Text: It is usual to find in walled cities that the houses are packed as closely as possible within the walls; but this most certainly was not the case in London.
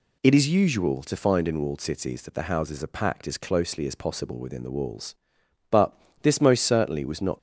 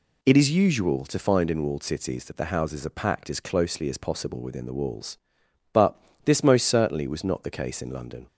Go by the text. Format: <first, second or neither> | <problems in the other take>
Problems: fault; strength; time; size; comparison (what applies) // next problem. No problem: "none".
second | pauses between "but" and "this"; slight; at 5.9 s; 0.26 s long; slight in the second // stops before "the case in London"; at 7.3 s